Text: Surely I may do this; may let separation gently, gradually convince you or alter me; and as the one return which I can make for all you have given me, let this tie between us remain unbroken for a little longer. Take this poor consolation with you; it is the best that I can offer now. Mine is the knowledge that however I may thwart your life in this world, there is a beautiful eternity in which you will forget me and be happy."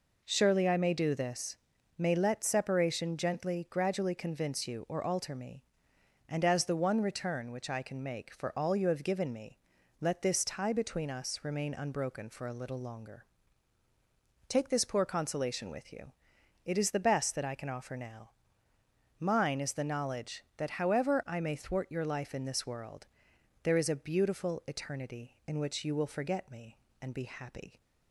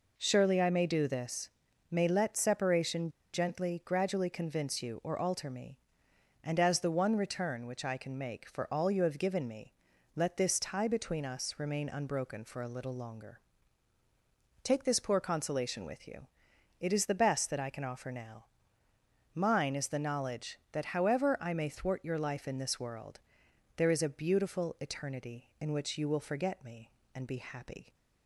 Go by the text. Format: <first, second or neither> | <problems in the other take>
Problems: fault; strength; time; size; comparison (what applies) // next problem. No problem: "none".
first | pauses between "separation" and "gently"; slight; at 3.0 s; 0.24 s long